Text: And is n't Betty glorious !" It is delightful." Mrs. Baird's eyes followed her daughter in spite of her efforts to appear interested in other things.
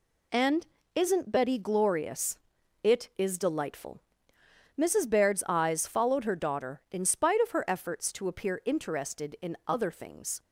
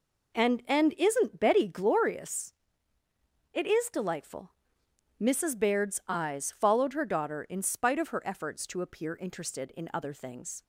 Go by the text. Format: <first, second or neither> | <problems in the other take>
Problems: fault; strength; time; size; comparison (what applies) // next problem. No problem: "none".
first | says "And" twice; at 0.6 s